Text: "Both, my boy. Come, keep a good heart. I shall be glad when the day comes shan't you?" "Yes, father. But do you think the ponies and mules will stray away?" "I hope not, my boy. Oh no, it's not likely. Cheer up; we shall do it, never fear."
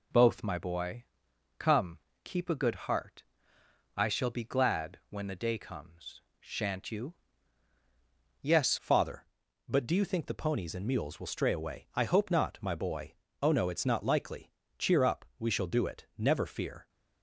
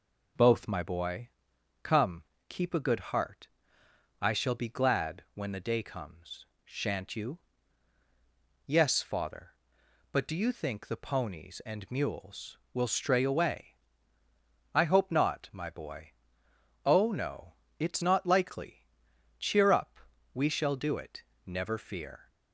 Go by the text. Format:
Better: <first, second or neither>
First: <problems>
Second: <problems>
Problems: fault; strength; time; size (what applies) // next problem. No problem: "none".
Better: second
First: pauses between "comes" and "shan't"; slight; at 6.1 s; 0.18 s long // changes voice at "father"; from 8.7 s on; 8.1 s long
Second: pauses between "comes" and "shan't"; slight; at 6.4 s; 0.18 s long